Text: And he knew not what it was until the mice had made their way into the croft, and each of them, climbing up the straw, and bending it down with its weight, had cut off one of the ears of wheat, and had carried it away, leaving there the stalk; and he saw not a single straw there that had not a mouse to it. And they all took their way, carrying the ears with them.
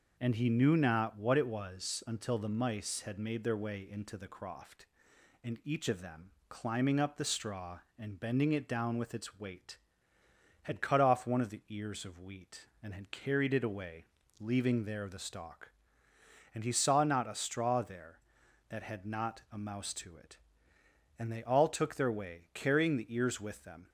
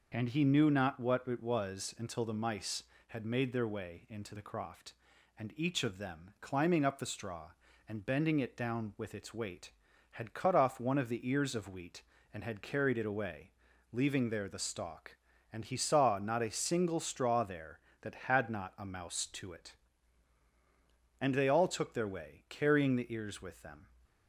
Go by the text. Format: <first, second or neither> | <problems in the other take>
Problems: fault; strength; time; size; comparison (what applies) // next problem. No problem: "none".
second | skips "single"; at 17.3 s